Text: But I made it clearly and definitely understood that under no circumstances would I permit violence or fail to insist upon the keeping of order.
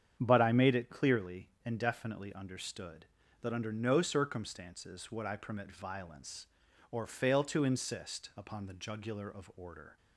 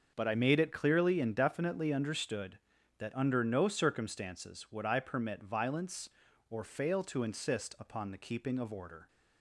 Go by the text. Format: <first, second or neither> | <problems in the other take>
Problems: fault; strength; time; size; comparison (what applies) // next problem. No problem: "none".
second | starts louder than the rest; strong; until 1.2 s; 8.5 dB; also in the second // says "jugular" for "keeping"; at 8.7 s